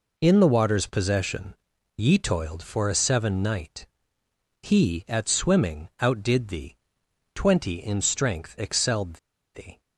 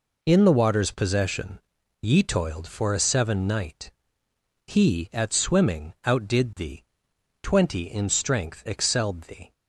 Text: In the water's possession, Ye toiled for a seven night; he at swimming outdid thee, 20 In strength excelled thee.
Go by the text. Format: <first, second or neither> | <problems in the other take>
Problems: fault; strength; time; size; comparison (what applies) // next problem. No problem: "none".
second | pauses between "excelled" and "thee"; at 9.1 s; 0.37 s long